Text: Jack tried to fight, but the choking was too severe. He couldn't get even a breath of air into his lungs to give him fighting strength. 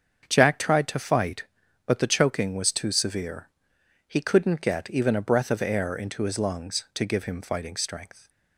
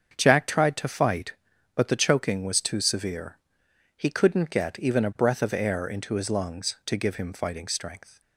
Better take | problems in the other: neither | starts louder than the rest; the same in both

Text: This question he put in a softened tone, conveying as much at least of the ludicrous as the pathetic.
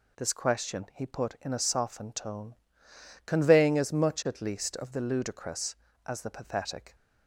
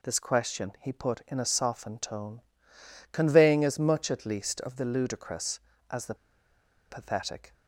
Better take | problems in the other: first | pauses between "the" and "pathetic"; noticeable; at 6.1 s; 0.74 s long

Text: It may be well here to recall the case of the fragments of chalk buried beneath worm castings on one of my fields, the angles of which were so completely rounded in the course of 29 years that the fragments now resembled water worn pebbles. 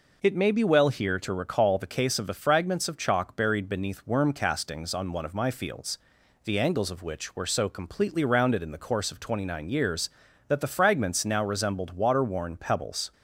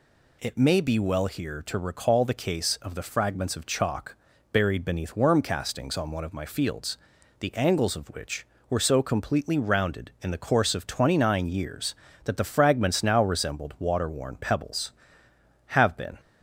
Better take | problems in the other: first | pauses between "chalk" and "buried"; at 4.1 s; 0.38 s long // goes on to say "have been"; from 15.6 s on; 0.54 s long

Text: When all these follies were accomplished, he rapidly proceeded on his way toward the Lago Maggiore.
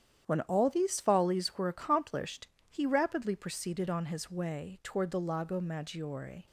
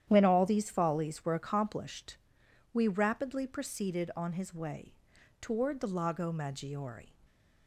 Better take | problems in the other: first | starts louder than the rest; strong; until 1.1 s; 10.5 dB; strong in the first // says "we" for "he"; at 2.7 s // pauses between "way" and "toward"; noticeable; at 4.9 s; 0.48 s long

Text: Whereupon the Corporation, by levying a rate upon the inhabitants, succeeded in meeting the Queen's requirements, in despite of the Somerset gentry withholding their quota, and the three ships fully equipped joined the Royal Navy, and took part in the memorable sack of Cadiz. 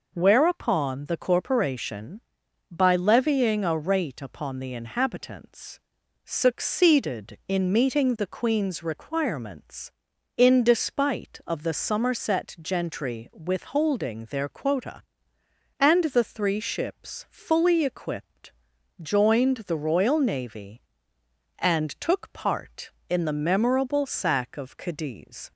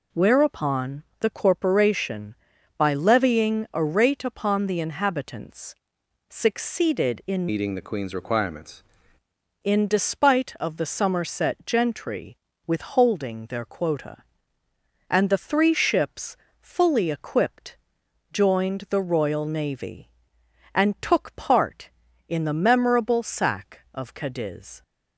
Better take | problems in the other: first | pauses between "Whereupon" and "the"; slight; at 1.0 s; 0.16 s long // changes voice from "meeting" to "requirements"; from 7.4 to 8.8 s; 1.4 s long // pauses between "gentry" and "withholding"; slight; at 12.3 s; 0.32 s long // pauses between "ships" and "fully"; slight; at 16.3 s; 0.24 s long // pauses between "equipped" and "joined"; noticeable; at 17.7 s; 0.56 s long; noticeable in the first

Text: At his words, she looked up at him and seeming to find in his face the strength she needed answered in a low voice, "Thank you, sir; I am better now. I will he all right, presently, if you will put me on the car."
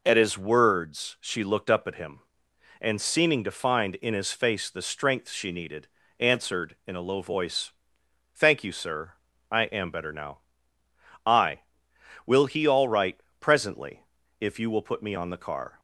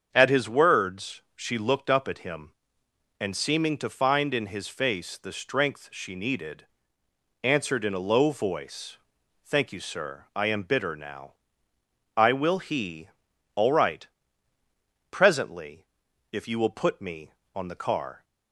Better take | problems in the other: first | starts louder than the rest; until 1.1 s; 7 dB // pauses between "needed" and "answered"; noticeable; at 6.6 s; 0.78 s long; slight in the first // says "bitter" for "better"; at 10.6 s // pauses between "he" and "all"; noticeable; at 13.0 s; 0.46 s long

